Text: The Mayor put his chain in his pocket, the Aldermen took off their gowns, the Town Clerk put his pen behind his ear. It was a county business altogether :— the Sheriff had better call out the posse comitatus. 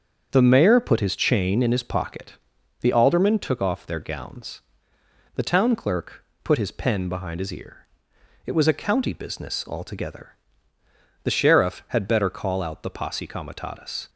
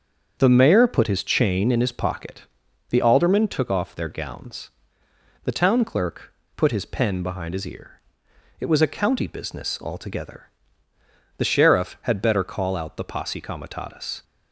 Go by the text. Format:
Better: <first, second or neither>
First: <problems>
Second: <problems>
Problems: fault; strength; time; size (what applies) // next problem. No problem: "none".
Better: neither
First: starts louder than the rest; strong; until 1.3 s; 7.5 dB // pauses between "Clerk" and "put"; slight; at 6.2 s; 0.20 s long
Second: starts louder than the rest; strong; until 1.4 s; 7 dB // pauses between "Clerk" and "put"; slight; at 6.3 s; 0.23 s long